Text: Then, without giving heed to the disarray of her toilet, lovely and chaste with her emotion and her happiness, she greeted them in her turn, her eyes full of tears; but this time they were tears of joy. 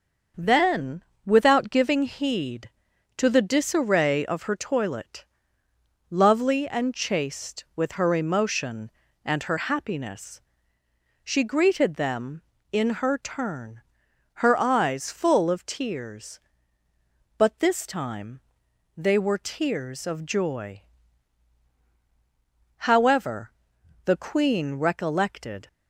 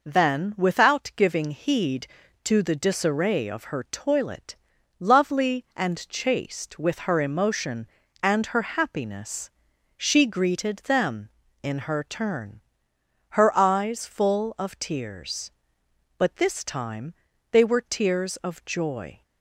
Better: second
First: starts louder than the rest; until 1.6 s; 6.5 dB // pauses between "time" and "they"; noticeable; at 18.3 s; 0.56 s long // goes on to say "However the queen recollected"; strong; from 22.7 s on; 2.9 s long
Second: pauses between "time" and "they"; at 17.1 s; 0.38 s long

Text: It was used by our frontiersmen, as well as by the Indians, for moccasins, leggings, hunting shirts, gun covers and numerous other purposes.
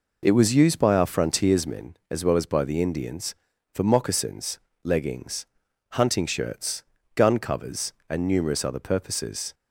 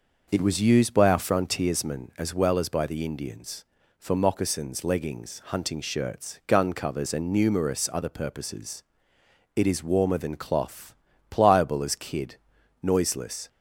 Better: first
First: none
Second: goes on to say "It is warmer than cloth pliable as kid noiseless"; strong; from 9.5 s on; 3.9 s long

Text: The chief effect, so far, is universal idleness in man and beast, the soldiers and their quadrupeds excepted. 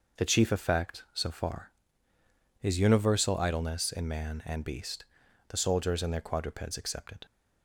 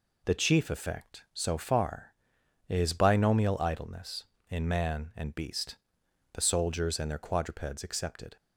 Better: first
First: none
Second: says "binomial" for "universal"; at 2.9 s

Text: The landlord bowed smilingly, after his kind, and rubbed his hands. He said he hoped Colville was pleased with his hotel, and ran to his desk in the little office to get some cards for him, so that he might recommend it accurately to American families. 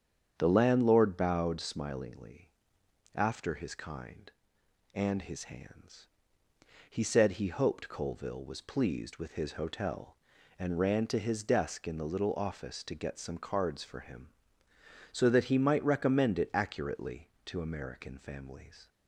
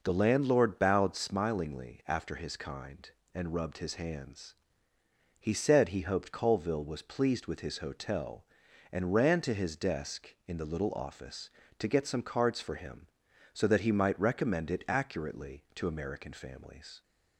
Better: second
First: starts louder than the rest; strong; until 1.4 s; 8 dB // skips "rubbed"; at 5.2 s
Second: none

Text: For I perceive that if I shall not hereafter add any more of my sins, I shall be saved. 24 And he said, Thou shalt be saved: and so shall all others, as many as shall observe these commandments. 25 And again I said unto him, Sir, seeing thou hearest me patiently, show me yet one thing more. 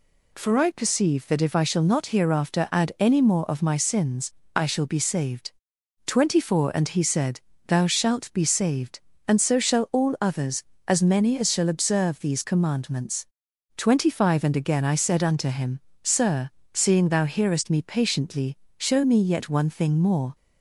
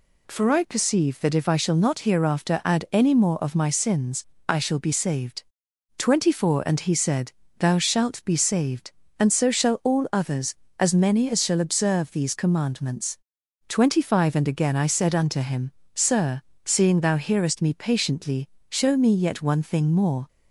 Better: neither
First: none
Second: none

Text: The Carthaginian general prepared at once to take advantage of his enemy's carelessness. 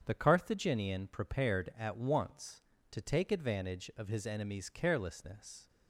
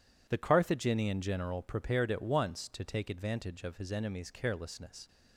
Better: second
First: starts louder than the rest; strong; until 1.0 s; 7.5 dB // skips "general"; at 1.0 s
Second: none

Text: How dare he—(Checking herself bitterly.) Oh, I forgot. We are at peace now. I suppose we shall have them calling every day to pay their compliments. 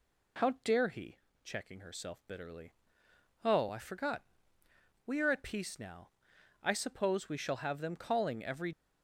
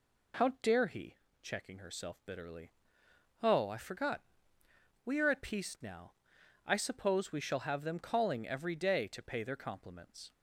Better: second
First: stops before "day to pay their compliments"; at 8.7 s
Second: none

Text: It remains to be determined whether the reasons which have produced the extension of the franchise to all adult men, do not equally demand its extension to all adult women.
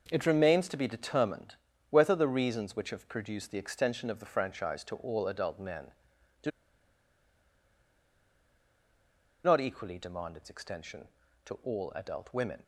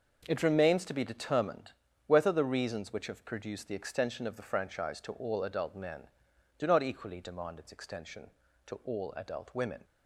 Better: second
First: pauses between "determined" and "whether"; slight; at 1.5 s; 0.34 s long // pauses between "do" and "not"; strong; at 6.5 s; 2.9 s long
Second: pauses between "determined" and "whether"; slight; at 1.7 s; 0.34 s long

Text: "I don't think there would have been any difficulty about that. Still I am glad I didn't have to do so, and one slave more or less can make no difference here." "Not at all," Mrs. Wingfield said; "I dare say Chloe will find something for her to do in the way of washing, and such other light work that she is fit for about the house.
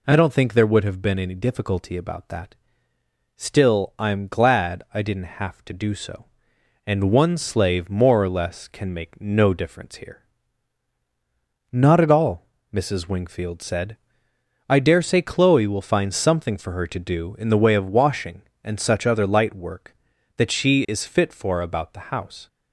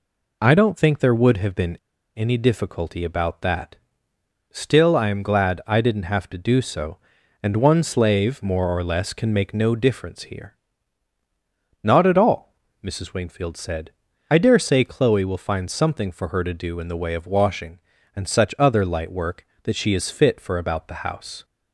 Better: first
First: none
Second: pauses between "been" and "any"; at 1.7 s; 0.39 s long

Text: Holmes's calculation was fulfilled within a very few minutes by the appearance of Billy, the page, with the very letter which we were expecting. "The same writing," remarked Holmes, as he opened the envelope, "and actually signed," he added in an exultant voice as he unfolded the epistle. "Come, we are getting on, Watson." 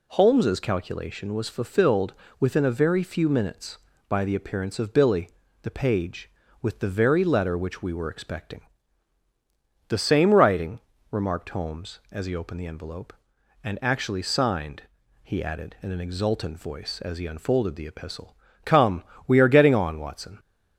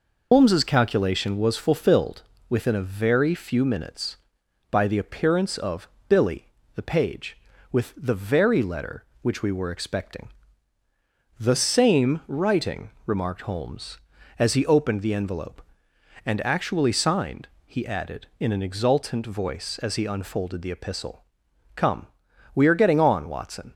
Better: first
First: pauses between "fulfilled" and "within"; slight; at 2.1 s; 0.26 s long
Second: loses the start of "Holmes's"; at 0.3 s; 110 ms // pauses between "fulfilled" and "within"; slight; at 2.2 s; 0.26 s long // pauses between "of" and "Billy"; slight; at 5.8 s; 0.20 s long

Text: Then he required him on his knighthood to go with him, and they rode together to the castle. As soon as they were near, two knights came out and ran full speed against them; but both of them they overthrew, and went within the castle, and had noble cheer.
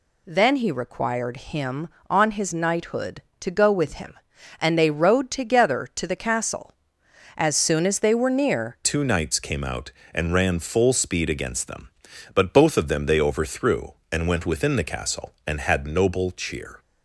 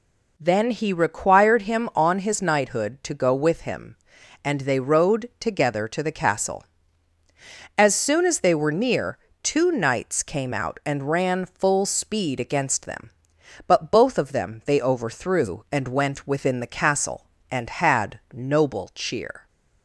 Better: second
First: changes voice at "two"; from 8.8 s on; 8.0 s long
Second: none

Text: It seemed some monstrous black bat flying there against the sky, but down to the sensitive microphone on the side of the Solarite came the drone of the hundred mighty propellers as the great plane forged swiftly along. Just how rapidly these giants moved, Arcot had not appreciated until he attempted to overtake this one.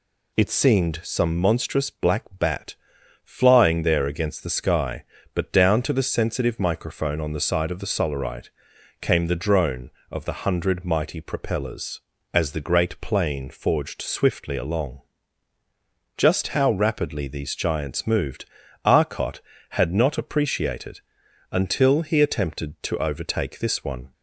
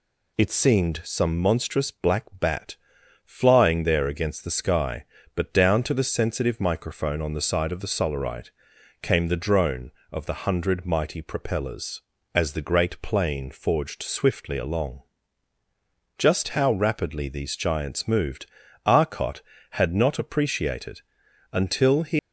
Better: first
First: pauses between "bat" and "flying"; noticeable; at 2.7 s; 0.48 s long // pauses between "Solarite" and "came"; noticeable; at 8.4 s; 0.50 s long // pauses between "appreciated" and "until"; noticeable; at 21.0 s; 0.50 s long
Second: pauses between "bat" and "flying"; noticeable; at 2.7 s; 0.48 s long // pauses between "Solarite" and "came"; noticeable; at 8.4 s; 0.50 s long // pauses between "appreciated" and "until"; noticeable; at 21.0 s; 0.50 s long // stops before "attempted to overtake this one"; at 22.1 s

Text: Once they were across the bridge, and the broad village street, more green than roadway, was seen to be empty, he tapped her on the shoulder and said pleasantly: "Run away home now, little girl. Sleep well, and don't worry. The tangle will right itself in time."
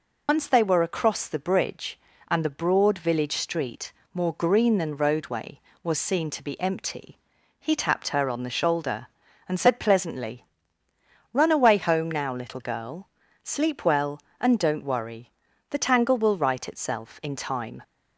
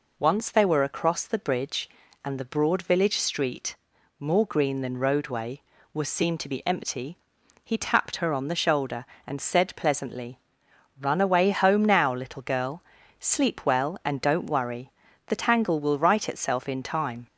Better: second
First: loses the start of "Once"; at 0.2 s; 70 ms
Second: none

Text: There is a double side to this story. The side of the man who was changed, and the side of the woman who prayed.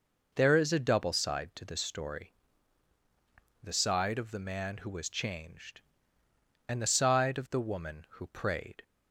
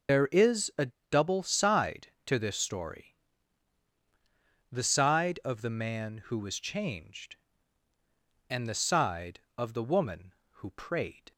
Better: first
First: none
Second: loses the start of "There"; at 0.0 s; 90 ms // starts louder than the rest; until 1.3 s; 6 dB // pauses between "a" and "double"; slight; at 0.8 s; 0.21 s long

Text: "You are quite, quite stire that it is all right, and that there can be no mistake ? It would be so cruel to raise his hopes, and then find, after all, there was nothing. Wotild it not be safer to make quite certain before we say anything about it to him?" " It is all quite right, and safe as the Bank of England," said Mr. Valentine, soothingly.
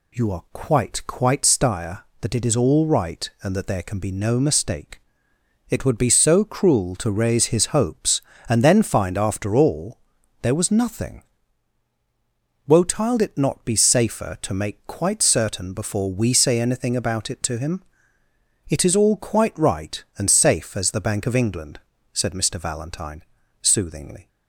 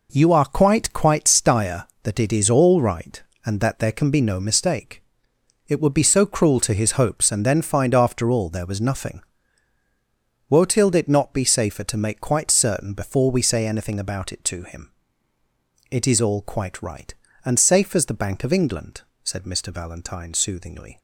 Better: first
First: none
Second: skips "raise"; at 6.7 s

